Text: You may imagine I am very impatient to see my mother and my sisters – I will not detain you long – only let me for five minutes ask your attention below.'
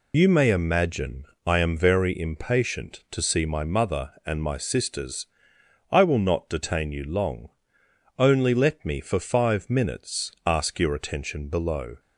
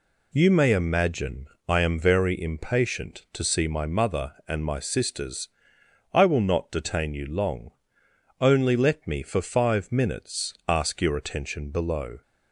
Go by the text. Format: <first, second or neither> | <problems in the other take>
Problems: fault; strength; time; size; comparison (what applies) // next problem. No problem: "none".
second | loses the start of "You"; at 0.1 s; 30 ms // pauses between "imagine" and "I"; slight; at 1.2 s; 0.20 s long; slight in the second // pauses between "minutes" and "ask"; slight; at 10.3 s; 0.16 s long; slight in the second